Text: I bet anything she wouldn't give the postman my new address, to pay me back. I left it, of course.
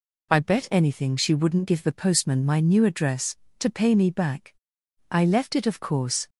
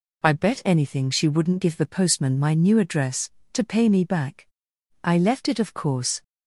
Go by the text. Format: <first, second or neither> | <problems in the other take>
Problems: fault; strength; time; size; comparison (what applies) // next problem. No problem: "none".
neither | none